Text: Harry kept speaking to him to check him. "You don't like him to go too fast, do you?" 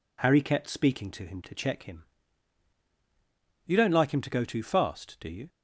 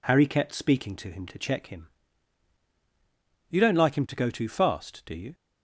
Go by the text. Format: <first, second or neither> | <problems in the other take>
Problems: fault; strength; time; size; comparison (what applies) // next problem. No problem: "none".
neither | none